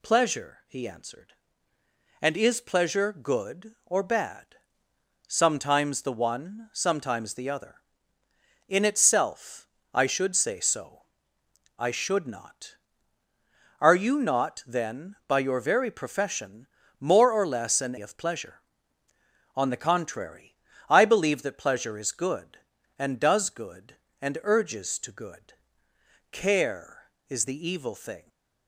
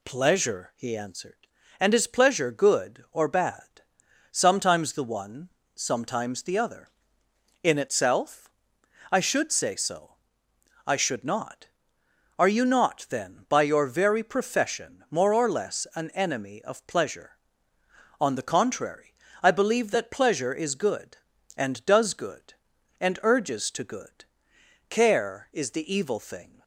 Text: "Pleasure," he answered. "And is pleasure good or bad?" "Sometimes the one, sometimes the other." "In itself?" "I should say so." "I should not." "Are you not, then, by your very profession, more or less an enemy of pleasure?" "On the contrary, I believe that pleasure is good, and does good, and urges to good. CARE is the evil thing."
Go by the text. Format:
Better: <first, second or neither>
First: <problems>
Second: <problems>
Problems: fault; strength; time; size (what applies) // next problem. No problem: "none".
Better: second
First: skips "enemy"; at 17.9 s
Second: none